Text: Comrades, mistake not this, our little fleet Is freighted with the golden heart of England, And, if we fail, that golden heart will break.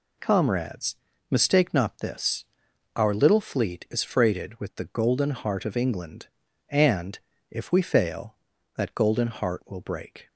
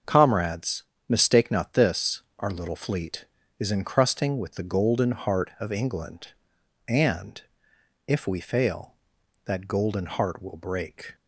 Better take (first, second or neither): first